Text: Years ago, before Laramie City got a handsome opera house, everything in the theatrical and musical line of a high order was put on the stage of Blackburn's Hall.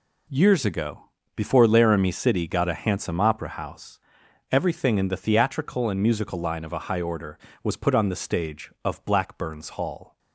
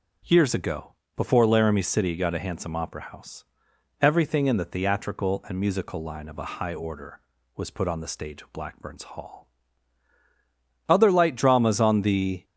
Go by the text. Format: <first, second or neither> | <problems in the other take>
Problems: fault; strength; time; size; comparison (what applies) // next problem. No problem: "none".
first | starts louder than the rest; noticeable; until 1.5 s; 6 dB // goes on to say "Other light dramas on the"; from 10.8 s on; 1.5 s long